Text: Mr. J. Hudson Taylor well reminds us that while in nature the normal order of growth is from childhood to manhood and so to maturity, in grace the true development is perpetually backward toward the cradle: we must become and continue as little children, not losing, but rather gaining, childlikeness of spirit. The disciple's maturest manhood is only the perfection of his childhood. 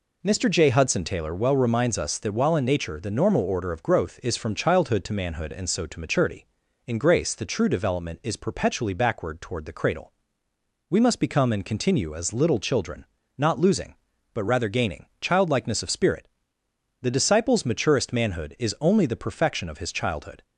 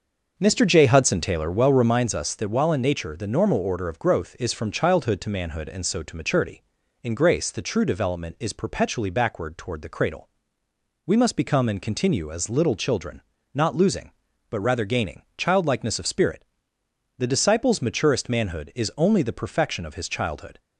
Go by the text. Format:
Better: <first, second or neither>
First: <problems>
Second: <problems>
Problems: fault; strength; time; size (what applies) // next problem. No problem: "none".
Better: first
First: none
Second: starts louder than the rest; noticeable; until 2.1 s; 6 dB